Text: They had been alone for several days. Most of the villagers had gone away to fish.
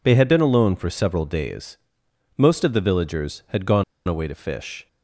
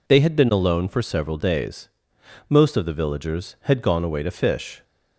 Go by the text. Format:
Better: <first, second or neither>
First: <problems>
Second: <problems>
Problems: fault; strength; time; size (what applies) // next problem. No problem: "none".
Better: second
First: pauses between "gone" and "away"; slight; at 3.8 s; 0.23 s long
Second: none